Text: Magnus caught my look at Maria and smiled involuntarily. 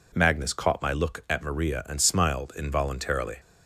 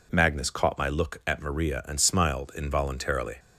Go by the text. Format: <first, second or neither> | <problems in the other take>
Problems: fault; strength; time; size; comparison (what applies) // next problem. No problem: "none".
neither | none